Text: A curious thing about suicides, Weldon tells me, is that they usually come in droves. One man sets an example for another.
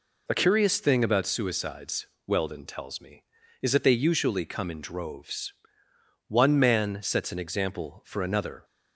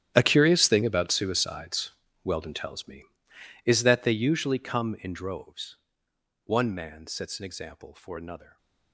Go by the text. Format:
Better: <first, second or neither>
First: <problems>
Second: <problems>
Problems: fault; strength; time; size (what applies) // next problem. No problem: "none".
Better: first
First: none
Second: gets quieter; strong; throughout; 17.5 dB // stays silent after the last word; slight; from 8.4 s on; 0.5 s long